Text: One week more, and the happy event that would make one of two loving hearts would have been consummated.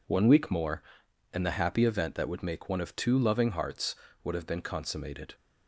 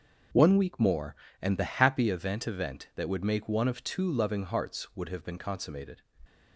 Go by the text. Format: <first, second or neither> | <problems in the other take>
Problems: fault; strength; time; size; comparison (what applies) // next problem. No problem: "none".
first | starts louder than the rest; until 1.6 s; 6.5 dB // says "event" twice; at 2.4 s